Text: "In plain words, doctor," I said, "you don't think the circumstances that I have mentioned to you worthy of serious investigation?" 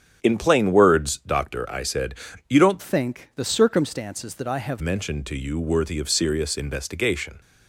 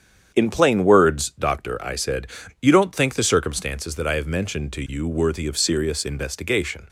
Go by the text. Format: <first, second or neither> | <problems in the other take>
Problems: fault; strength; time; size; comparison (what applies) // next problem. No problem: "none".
second | starts louder than the rest; strong; until 1.2 s; 8.5 dB; strong in the second // changes voice from "think" to "have"; from 2.8 to 4.8 s; 2.0 s long